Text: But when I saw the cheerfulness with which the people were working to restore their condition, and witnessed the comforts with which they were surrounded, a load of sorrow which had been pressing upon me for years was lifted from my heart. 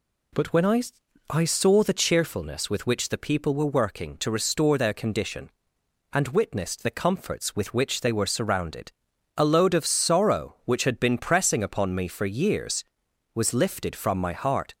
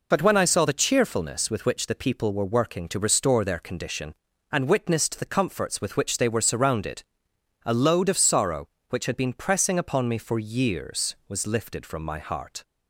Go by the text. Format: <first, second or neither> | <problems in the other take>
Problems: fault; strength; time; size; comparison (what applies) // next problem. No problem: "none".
second | says "I" twice; at 1.2 s